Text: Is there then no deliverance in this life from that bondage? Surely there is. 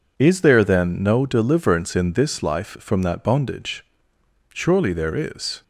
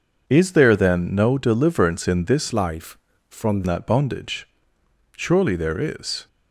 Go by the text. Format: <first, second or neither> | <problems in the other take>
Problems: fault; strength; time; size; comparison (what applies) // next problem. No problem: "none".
first | changes voice from "life" to "from"; from 2.5 to 3.6 s; 1.1 s long